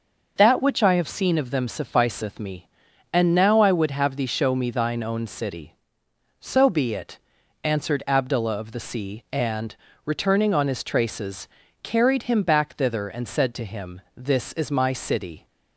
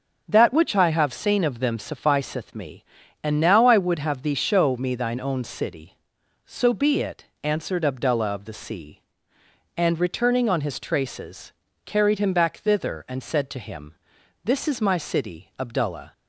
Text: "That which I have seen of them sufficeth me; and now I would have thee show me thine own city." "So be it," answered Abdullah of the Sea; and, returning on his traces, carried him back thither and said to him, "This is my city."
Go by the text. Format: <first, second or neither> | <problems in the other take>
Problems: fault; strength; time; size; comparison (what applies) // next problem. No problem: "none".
first | starts louder than the rest; noticeable; until 1.2 s; 6 dB // goes on to say "Abdullah"; from 15.5 s on; 0.54 s long